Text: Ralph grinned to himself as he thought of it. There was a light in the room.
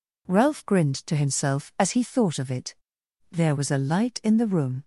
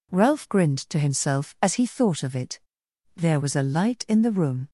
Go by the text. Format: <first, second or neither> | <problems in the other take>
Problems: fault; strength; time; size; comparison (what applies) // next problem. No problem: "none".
neither | none